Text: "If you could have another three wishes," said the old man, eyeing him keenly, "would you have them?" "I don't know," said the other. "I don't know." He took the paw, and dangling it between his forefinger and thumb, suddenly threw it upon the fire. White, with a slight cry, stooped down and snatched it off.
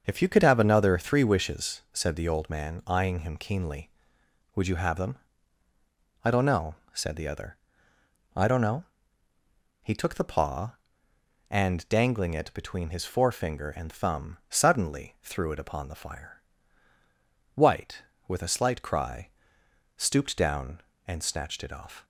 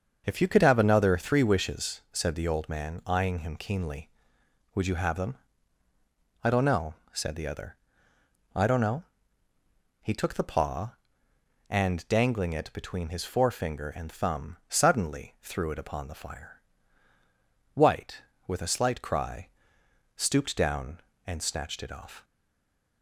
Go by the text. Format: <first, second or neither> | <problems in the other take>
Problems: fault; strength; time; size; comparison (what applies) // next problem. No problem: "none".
first | starts louder than the rest; until 1.2 s; 6.5 dB; also in the first // stays silent after the last word; slight; from 22.2 s on; 0.8 s long